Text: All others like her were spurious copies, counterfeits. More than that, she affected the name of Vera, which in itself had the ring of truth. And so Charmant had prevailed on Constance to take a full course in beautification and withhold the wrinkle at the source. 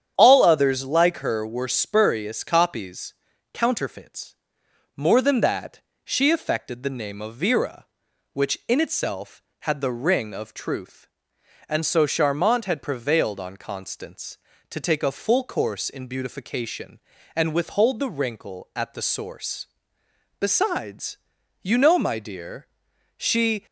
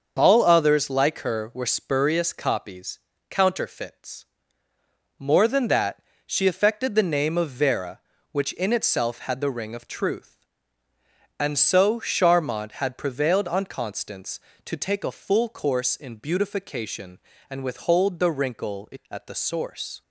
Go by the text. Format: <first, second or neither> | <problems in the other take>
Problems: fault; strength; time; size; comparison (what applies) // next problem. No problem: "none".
second | starts louder than the rest; strong; until 1.1 s; 8.5 dB; also in the second // goes on to say "Besides you know my dear she"; strong; from 20.3 s on; 3.2 s long